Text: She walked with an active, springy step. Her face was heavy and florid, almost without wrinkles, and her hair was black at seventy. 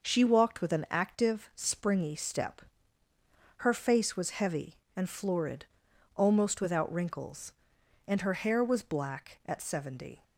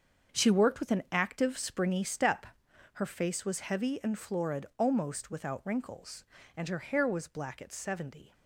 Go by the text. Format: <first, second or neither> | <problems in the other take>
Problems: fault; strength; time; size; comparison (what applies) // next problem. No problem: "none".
first | starts louder than the rest; until 1.4 s; 7 dB // says "worked" for "walked"; at 0.5 s